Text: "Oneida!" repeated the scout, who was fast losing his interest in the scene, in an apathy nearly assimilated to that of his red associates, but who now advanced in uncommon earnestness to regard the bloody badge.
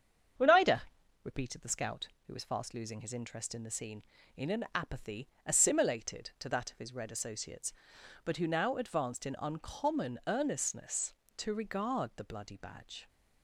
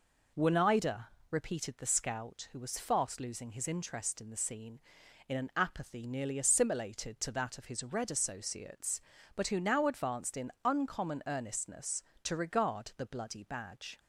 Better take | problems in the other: second | starts louder than the rest; strong; until 1.8 s; 7.5 dB // skips "nearly"; at 5.3 s

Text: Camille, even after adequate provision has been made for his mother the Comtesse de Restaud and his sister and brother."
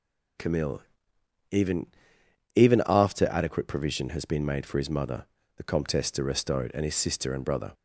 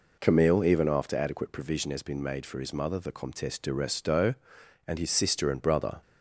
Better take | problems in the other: second | says "even" twice; at 2.5 s // pauses between "mother" and "the"; slight; at 5.2 s; 0.32 s long

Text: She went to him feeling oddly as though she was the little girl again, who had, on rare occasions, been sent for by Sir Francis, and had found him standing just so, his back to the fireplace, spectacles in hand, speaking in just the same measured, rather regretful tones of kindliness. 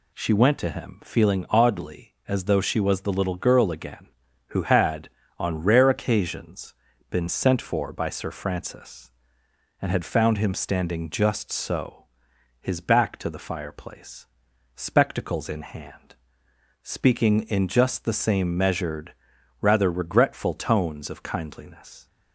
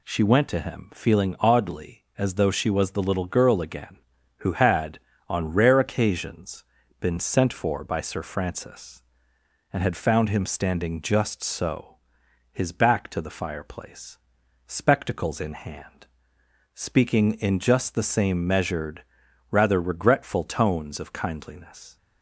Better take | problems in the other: neither | none

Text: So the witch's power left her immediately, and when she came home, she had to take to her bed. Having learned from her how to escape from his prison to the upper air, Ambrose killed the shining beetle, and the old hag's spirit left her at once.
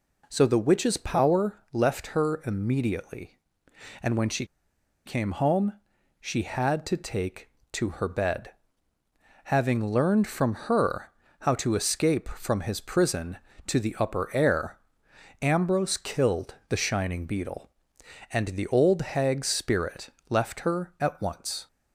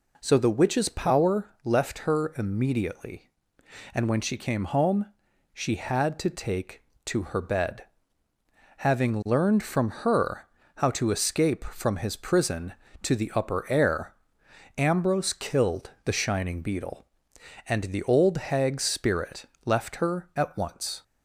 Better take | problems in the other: second | pauses between "she" and "came"; noticeable; at 4.4 s; 0.61 s long // pauses between "her" and "how"; slight; at 11.1 s; 0.30 s long; slight in the second // pauses between "spirit" and "left"; slight; at 20.0 s; 0.20 s long; slight in the second

